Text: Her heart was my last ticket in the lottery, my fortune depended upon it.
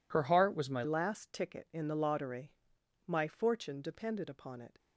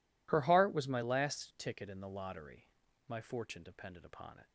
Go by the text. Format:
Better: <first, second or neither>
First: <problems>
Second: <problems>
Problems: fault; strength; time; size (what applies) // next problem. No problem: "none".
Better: second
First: changes voice at "last"; from 0.8 s on; 3.9 s long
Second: none